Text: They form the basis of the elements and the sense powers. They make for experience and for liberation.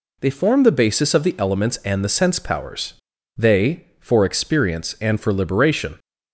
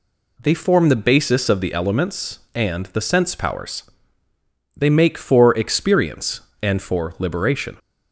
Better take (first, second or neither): second